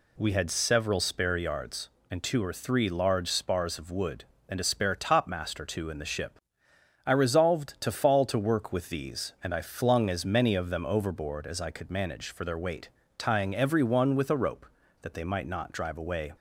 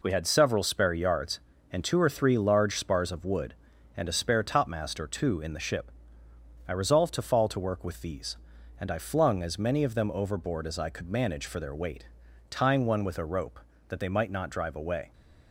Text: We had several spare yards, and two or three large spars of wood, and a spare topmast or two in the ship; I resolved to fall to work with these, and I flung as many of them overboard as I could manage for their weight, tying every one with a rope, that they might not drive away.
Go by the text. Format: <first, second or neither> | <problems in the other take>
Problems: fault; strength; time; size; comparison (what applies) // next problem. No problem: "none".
first | skips "every"; at 12.8 s